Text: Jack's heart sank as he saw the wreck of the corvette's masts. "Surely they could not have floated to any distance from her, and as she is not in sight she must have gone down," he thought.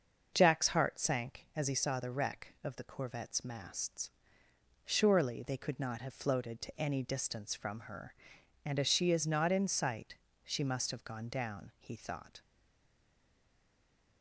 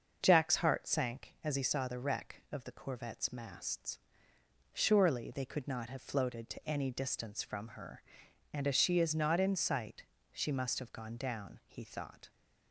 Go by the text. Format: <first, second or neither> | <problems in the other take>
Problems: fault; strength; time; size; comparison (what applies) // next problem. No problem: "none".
second | starts louder than the rest; until 1.3 s; 6.5 dB; also in the second // pauses between "sight" and "she"; slight; at 10.1 s; 0.28 s long; slight in the second // stays silent after the last word; noticeable; from 12.4 s on; 1.8 s long